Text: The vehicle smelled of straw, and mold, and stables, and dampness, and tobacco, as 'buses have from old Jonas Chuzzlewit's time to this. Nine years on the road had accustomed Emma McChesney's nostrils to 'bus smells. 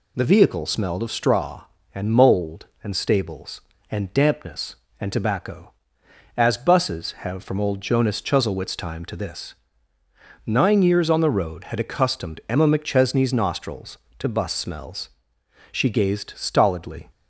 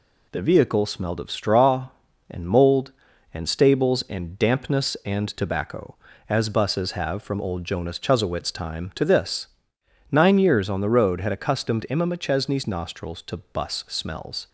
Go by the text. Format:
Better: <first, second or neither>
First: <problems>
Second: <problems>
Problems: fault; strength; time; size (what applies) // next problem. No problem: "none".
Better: second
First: goes on to say "She gazed stolidly"; from 15.7 s on; 1.3 s long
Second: none